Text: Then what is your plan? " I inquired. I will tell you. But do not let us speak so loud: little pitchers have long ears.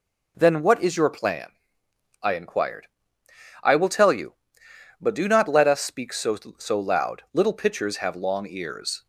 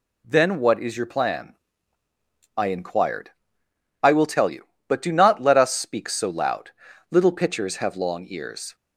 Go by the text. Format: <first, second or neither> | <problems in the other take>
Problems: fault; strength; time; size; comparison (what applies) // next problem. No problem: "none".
second | says "so" twice; at 6.5 s